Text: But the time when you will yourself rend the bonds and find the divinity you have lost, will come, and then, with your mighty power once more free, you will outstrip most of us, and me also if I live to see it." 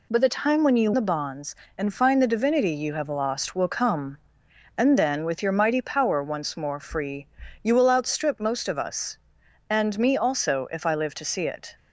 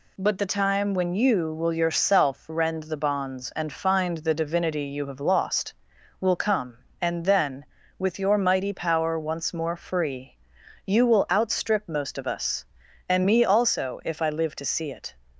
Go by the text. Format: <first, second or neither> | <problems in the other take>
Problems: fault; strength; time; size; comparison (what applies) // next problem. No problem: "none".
second | skips "will yourself rend"; at 0.9 s